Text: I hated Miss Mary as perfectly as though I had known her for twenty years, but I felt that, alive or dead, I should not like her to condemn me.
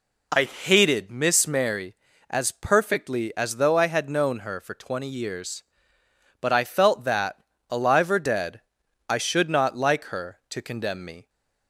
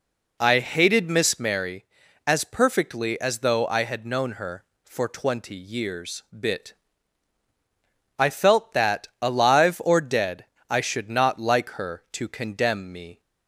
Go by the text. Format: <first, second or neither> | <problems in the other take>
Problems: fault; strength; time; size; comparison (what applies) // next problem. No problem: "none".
first | says "bit" for "but"; at 6.3 s